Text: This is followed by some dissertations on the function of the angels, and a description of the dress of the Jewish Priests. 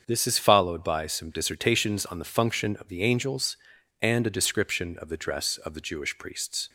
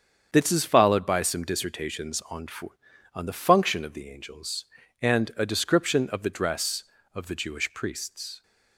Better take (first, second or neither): first